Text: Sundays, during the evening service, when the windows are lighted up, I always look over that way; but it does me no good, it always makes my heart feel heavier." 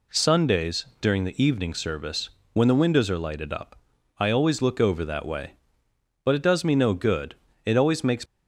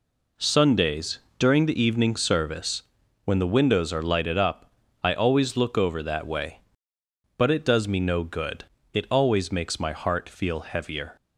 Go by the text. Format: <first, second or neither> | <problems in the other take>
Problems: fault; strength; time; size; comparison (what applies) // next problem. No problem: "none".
second | stops before "my heart feel heavier"; at 8.2 s